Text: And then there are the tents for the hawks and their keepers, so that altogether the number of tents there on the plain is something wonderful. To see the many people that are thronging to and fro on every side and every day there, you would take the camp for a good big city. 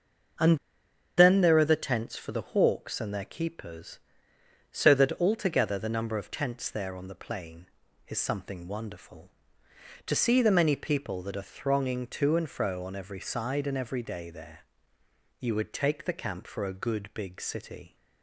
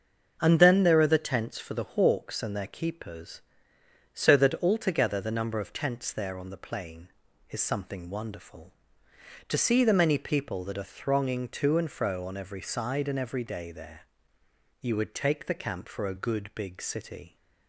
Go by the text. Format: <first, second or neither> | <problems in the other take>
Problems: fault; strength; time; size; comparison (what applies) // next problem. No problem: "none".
second | starts louder than the rest; until 2.0 s; 6.5 dB; also in the second // pauses between "And" and "then"; noticeable; at 0.5 s; 0.60 s long